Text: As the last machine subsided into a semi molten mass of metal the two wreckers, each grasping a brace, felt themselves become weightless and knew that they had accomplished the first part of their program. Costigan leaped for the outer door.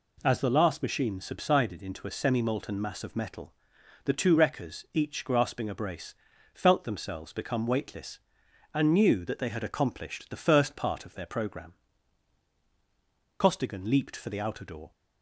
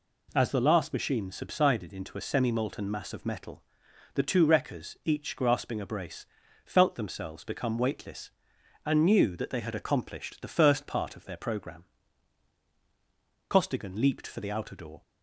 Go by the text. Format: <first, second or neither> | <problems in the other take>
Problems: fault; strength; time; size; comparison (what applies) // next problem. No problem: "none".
neither | pauses between "metal" and "the"; noticeable; the same in both